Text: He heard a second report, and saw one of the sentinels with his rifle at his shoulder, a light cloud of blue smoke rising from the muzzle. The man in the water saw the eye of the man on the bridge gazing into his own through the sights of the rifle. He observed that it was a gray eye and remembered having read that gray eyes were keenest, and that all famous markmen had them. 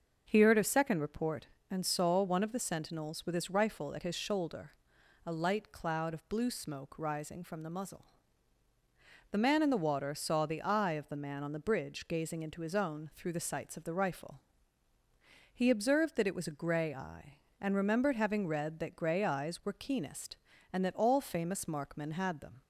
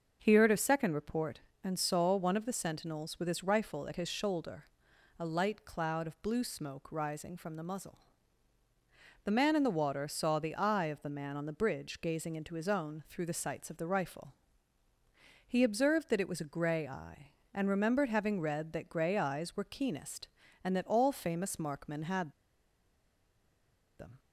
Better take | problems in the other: first | starts louder than the rest; until 1.2 s; 6 dB; also in the first // pauses between "had" and "them"; strong; at 22.3 s; 1.6 s long

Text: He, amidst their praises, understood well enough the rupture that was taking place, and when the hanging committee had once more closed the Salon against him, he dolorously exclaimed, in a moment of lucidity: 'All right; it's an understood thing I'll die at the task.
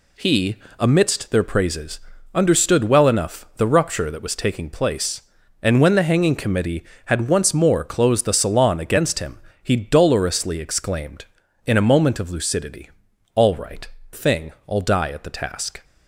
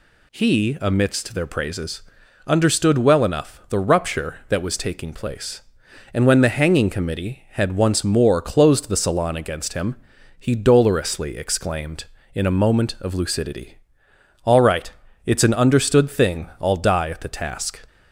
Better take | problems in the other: second | skips "it's an understood"; at 14.0 s

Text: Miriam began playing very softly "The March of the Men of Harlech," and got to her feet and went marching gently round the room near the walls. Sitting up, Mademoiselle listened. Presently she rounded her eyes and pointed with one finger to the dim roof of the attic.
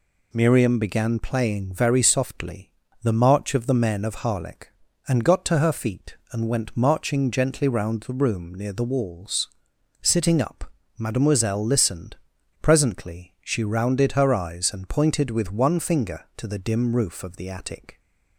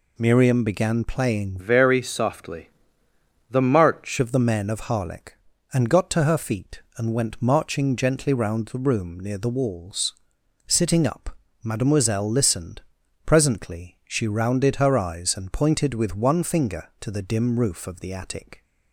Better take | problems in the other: first | changes voice from "very" to "March"; from 1.5 to 4.1 s; 2.6 s long // pauses between "softly" and "The"; noticeable; at 2.6 s; 0.82 s long; slight in the first

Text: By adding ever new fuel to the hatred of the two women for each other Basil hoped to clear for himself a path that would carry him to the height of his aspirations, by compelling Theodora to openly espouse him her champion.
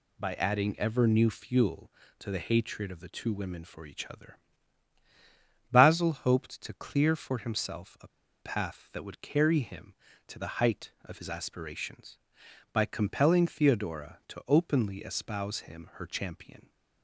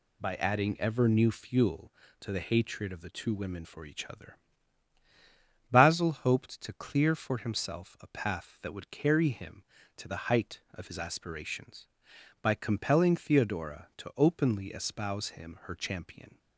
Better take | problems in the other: second | pauses between "other" and "Basil"; strong; at 4.3 s; 1.3 s long; strong in the second // pauses between "a" and "path"; slight; at 8.0 s; 0.32 s long

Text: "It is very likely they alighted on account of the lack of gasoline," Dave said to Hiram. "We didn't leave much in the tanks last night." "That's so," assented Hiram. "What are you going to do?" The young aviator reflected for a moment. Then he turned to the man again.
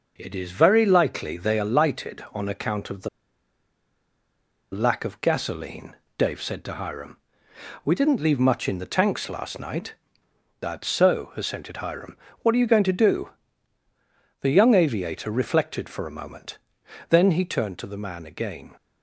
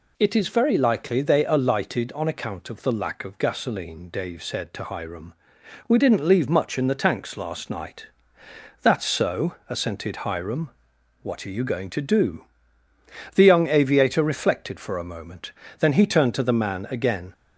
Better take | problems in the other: second | pauses between "the" and "lack"; strong; at 3.0 s; 1.6 s long

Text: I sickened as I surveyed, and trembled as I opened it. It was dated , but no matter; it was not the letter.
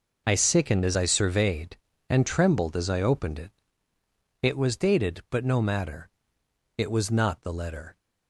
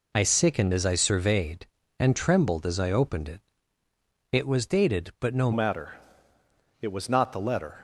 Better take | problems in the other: first | changes voice at "matter"; from 5.5 s on; 2.3 s long

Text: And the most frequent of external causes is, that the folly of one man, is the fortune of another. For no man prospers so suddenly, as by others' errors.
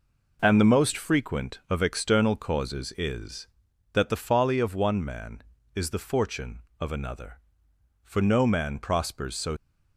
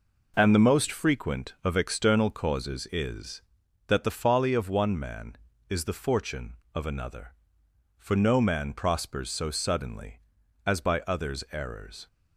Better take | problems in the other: second | stops before "suddenly as by others errors"; at 9.5 s

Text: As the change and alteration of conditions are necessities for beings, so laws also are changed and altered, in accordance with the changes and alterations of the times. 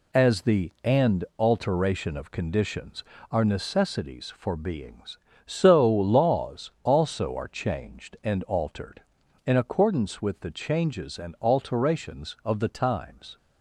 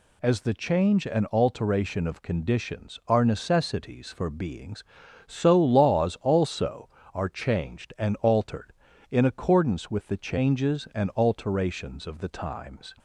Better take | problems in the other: second | skips "change"; at 0.7 s // pauses between "and" and "alteration"; slight; at 1.2 s; 0.16 s long

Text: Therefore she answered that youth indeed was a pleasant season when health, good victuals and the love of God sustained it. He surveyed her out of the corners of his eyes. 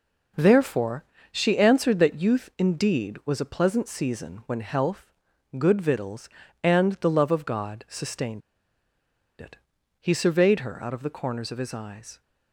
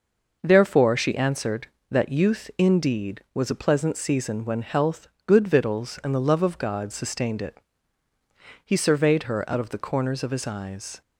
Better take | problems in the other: second | pauses between "Therefore" and "she"; slight; at 1.0 s; 0.28 s long // pauses between "sustained" and "it"; at 8.4 s; 0.98 s long

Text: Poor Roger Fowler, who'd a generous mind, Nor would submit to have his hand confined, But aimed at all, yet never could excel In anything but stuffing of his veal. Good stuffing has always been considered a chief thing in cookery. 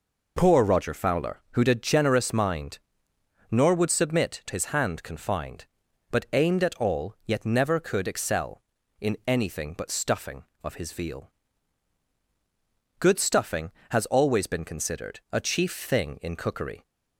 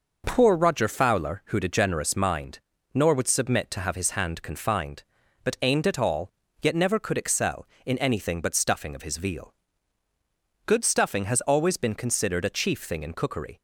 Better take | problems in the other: second | skips "have"; at 4.4 s

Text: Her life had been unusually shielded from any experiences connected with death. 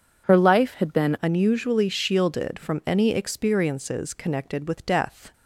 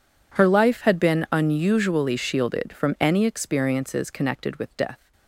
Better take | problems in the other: second | changes voice at "unusually"; from 1.2 s on; 4.1 s long

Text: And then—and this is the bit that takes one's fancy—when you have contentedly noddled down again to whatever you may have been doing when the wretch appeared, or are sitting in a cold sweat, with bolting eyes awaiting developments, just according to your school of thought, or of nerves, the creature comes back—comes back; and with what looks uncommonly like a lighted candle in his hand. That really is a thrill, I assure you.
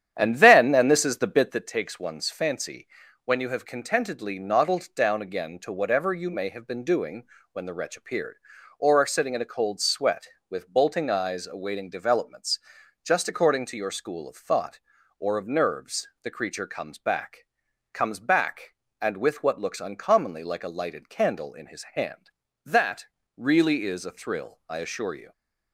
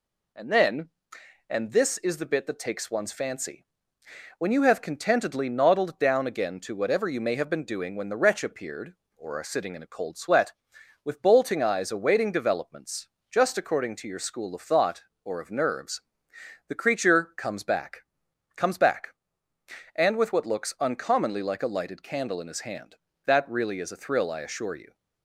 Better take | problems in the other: second | starts louder than the rest; strong; until 1.6 s; 10 dB // pauses between "doing" and "when"; slight; at 7.2 s; 0.30 s long // pauses between "That" and "really"; slight; at 23.0 s; 0.30 s long

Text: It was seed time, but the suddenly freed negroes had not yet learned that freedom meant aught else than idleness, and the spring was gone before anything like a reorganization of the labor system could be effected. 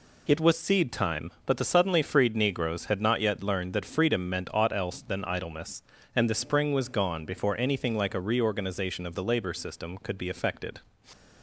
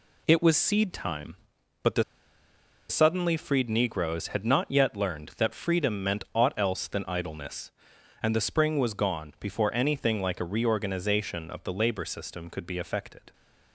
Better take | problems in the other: first | pauses between "the" and "suddenly"; noticeable; at 2.0 s; 0.86 s long

